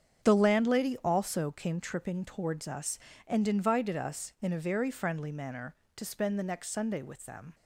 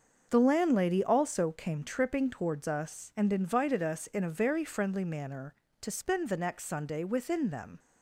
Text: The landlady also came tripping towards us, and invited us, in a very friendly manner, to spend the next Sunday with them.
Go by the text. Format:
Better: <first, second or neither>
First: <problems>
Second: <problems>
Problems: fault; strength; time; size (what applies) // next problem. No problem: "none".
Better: first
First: starts louder than the rest; strong; until 1.3 s; 7.5 dB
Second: starts louder than the rest; until 1.3 s; 6.5 dB // says "within" for "with"; at 7.0 s